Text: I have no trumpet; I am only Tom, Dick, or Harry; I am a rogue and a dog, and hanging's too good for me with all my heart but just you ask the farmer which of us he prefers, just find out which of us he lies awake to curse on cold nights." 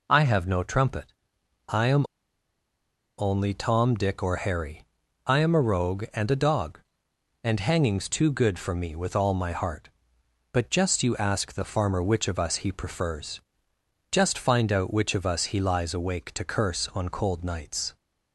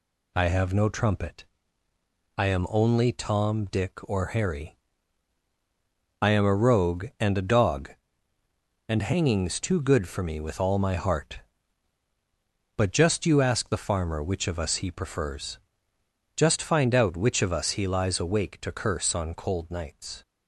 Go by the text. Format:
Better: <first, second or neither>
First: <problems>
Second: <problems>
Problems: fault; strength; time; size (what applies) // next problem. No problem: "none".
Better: second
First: pauses between "am" and "only"; at 2.0 s; 1.1 s long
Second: none